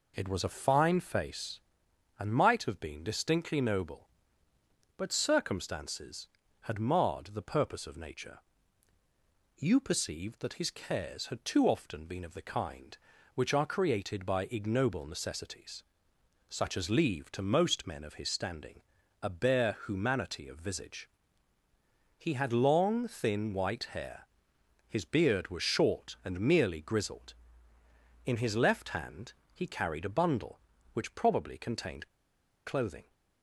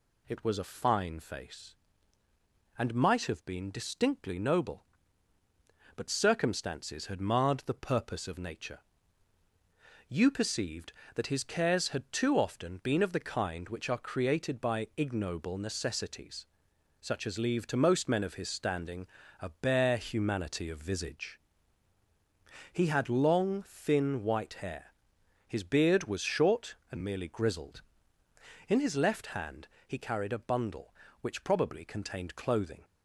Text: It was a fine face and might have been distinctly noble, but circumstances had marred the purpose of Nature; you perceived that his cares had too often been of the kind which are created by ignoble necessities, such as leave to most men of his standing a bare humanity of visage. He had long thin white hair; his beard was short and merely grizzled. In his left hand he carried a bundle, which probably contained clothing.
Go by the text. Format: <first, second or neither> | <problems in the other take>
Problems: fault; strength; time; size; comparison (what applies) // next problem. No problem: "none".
second | pauses between "standing" and "a"; at 18.8 s; 0.40 s long; slight in the second // pauses between "hand" and "he"; slight; at 29.3 s; 0.20 s long; slight in the second // pauses between "contained" and "clothing"; noticeable; at 32.0 s; 0.57 s long